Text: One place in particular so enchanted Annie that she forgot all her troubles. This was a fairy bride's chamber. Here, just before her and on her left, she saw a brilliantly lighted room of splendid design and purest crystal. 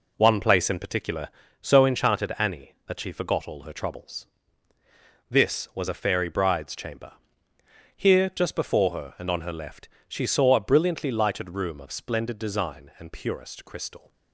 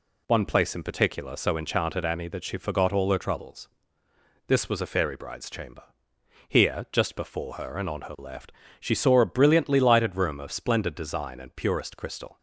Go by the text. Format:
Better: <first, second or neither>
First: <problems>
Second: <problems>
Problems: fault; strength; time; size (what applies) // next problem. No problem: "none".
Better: second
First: starts louder than the rest; until 2.0 s; 3.5 dB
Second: none